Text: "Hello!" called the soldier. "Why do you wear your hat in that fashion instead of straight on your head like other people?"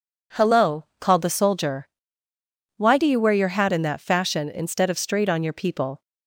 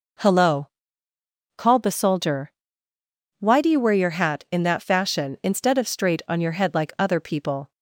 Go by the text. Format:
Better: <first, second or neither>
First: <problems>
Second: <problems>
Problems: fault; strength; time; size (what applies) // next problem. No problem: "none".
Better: second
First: skips "head like other"; at 5.5 s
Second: none